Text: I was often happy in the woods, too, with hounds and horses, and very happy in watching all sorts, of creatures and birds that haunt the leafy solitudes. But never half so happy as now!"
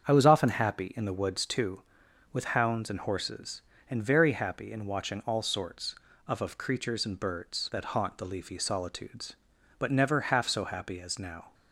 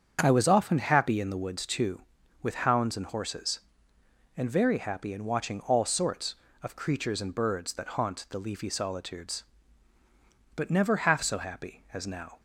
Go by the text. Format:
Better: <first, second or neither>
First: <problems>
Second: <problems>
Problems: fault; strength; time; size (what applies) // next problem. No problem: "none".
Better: second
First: starts louder than the rest; strong; until 1.1 s; 7.5 dB // says "of" twice; at 6.4 s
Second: starts louder than the rest; strong; until 1.2 s; 7.5 dB